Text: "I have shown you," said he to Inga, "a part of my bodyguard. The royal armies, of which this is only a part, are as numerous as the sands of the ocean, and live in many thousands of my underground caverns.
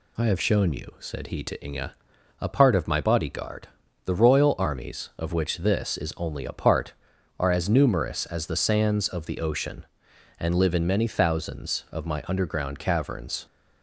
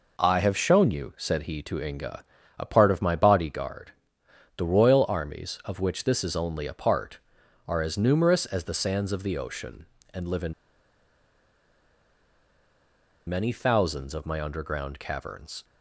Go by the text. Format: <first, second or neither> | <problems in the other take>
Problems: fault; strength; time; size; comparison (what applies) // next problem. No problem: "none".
first | pauses between "in" and "many"; strong; at 10.5 s; 2.7 s long